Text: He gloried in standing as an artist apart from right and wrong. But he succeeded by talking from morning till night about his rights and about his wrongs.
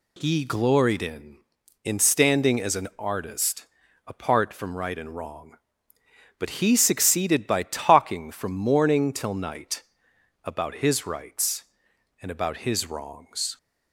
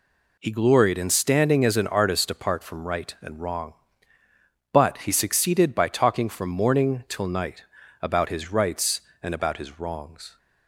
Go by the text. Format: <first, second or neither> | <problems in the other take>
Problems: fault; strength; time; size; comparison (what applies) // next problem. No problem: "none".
second | says "in" twice; at 1.8 s // pauses between "artist" and "apart"; at 3.6 s; 0.40 s long // pauses between "night" and "about"; noticeable; at 9.8 s; 0.60 s long; also in the second